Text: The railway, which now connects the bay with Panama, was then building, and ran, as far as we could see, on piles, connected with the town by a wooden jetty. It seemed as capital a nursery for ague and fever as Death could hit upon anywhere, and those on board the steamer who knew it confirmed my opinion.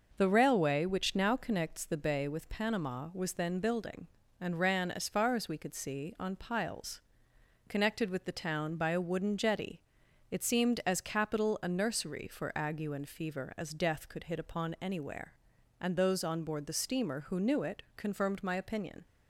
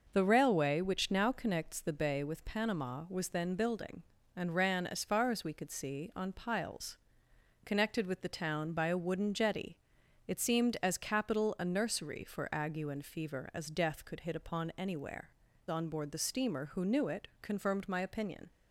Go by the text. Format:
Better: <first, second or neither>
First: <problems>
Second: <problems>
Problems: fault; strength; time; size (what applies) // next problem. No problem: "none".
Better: first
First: none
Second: skips "and those"; at 15.5 s